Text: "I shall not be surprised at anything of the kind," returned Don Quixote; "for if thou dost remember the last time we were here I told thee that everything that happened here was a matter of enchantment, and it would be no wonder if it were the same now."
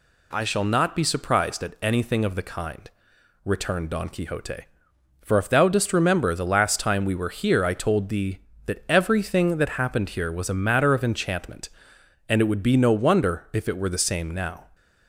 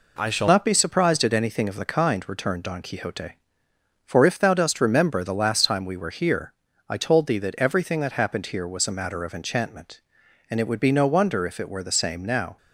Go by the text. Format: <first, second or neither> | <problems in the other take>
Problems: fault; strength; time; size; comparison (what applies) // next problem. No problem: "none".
first | changes voice at "not"; from 0.4 s on; 12.1 s long // pauses between "here" and "I"; slight; at 6.5 s; 0.36 s long